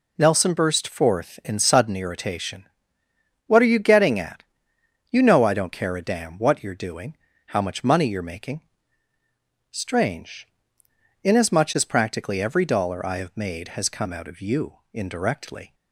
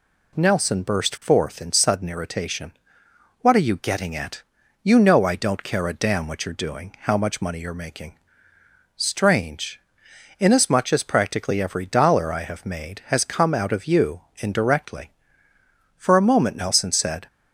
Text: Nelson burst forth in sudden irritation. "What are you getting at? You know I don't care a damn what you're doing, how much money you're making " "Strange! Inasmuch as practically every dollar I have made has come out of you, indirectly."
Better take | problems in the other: first | goes on to say "For a moment Nelson said"; noticeable; from 15.9 s on; 1.3 s long

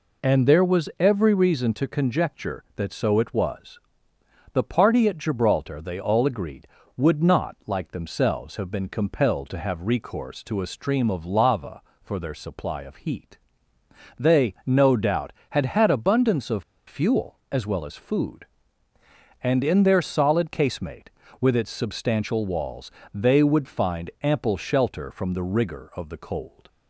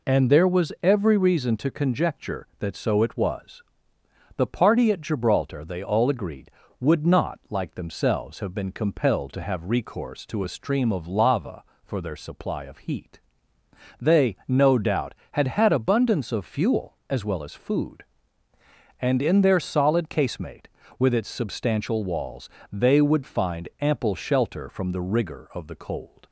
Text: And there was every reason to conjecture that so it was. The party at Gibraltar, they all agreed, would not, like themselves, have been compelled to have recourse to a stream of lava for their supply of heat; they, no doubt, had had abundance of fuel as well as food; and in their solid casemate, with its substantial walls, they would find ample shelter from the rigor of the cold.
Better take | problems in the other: second | pauses between "of" and "fuel"; slight; at 16.6 s; 0.24 s long

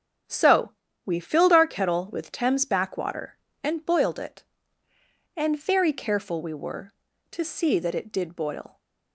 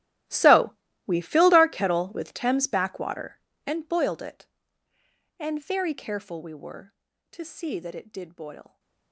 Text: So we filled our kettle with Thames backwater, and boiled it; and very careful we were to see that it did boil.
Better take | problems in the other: first | gets quieter; strong; throughout; 20.5 dB // starts louder than the rest; strong; until 1.6 s; 14.5 dB; strong in the first // pauses between "So" and "we"; slight; at 0.7 s; 0.34 s long; slight in the first

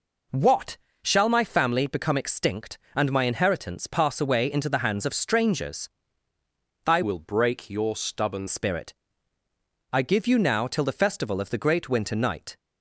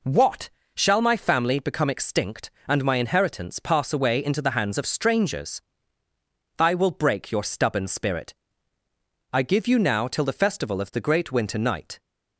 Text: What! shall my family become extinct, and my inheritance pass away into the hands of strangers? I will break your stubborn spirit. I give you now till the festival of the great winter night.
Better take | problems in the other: second | changes voice from "will" to "stubborn"; from 7.0 to 8.4 s; 1.4 s long

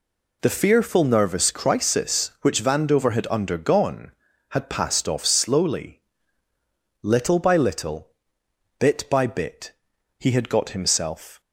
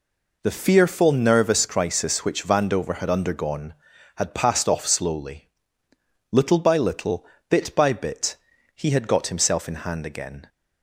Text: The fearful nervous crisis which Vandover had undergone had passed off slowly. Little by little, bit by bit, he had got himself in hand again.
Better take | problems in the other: second | stops before "in hand again"; at 11.4 s

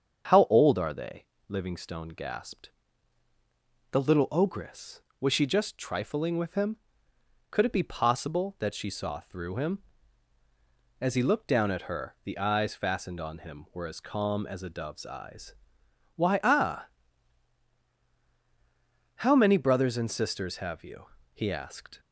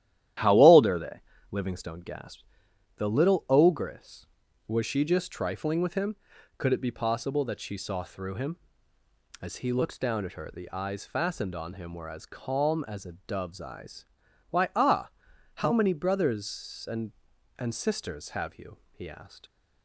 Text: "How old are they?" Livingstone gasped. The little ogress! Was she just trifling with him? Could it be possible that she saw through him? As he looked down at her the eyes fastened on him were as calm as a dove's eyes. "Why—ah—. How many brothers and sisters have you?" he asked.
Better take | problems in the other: first | starts louder than the rest; strong; until 1.7 s; 12 dB; strong in the first // says "and" twice; at 17.5 s

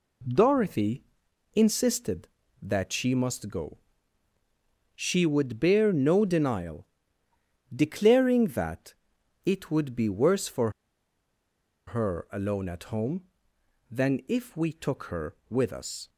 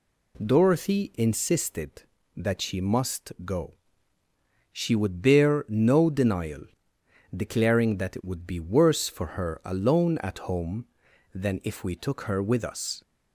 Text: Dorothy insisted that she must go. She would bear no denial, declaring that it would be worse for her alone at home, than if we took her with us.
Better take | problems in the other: second | pauses between "Dorothy" and "insisted"; noticeable; at 1.0 s; 0.52 s long // pauses between "that" and "it"; noticeable; at 8.9 s; 0.50 s long // pauses between "for" and "her"; at 10.7 s; 1.1 s long

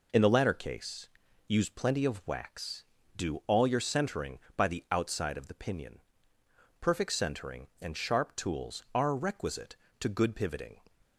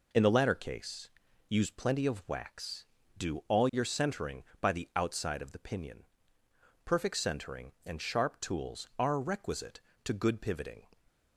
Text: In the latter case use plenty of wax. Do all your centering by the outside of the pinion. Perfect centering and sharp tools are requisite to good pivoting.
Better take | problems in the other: neither | pauses between "case" and "use"; the same in both

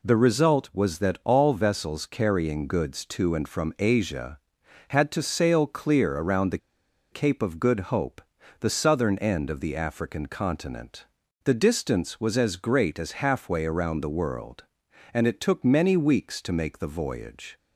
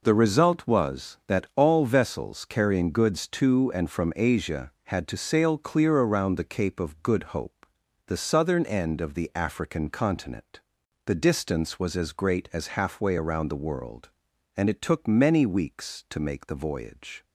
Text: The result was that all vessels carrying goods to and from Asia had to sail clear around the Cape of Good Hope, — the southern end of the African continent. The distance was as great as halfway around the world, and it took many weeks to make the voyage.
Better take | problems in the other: second | pauses between "the" and "Cape"; noticeable; at 6.5 s; 0.53 s long

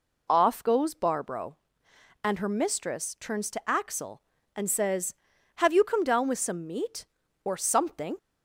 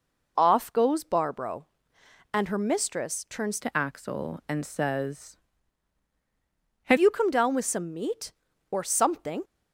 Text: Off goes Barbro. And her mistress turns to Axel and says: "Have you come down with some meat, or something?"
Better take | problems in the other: first | changes voice from "to" to "Have"; from 3.6 to 6.9 s; 3.3 s long

